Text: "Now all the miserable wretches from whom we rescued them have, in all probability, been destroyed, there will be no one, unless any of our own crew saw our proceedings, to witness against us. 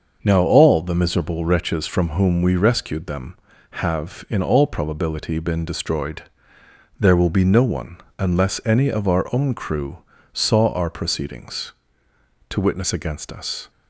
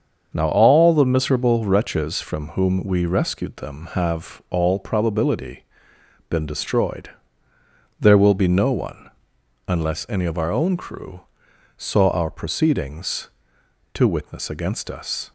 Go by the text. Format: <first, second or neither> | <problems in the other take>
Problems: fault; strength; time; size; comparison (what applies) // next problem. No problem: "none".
first | starts louder than the rest; until 1.3 s; 7 dB; also in the first // skips "in"; at 4.4 s // pauses between "crew" and "saw"; noticeable; at 11.2 s; 0.54 s long; slight in the first